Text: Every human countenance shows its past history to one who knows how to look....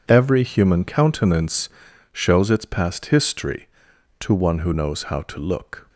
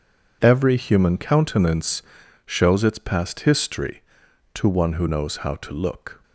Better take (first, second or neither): neither